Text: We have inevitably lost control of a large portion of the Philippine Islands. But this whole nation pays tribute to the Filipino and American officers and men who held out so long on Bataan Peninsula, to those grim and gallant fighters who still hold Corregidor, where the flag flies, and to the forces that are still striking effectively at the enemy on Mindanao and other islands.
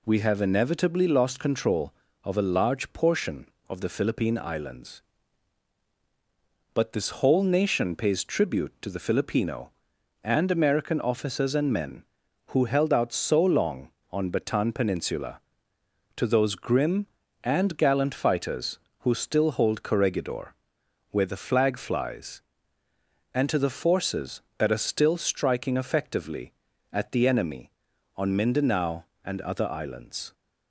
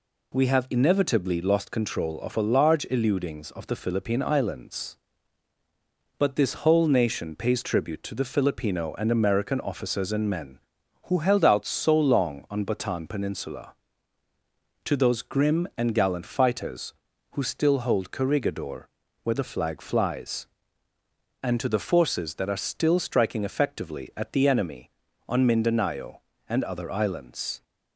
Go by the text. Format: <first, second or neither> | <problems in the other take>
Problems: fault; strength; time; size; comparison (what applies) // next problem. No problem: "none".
first | says "eludings" for "portion"; at 2.8 s